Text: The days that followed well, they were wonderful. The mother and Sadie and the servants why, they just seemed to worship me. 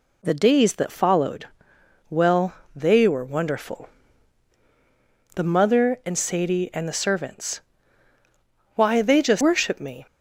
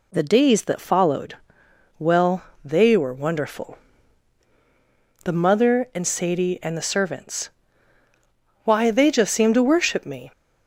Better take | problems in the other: second | pauses between "followed" and "well"; noticeable; at 1.4 s; 0.60 s long; noticeable in the second // pauses between "servants" and "why"; at 7.5 s; 1.1 s long; also in the second // skips "seemed to"; at 9.4 s

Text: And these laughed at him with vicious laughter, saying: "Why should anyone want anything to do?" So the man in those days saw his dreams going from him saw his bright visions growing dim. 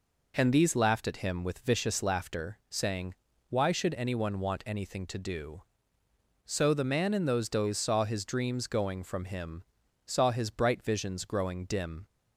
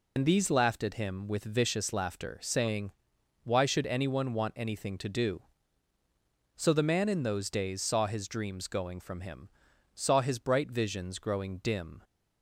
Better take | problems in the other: first | loses the start of "And"; at 0.1 s; 75 ms // pauses between "him" and "saw"; at 9.5 s; 0.44 s long; also in the first

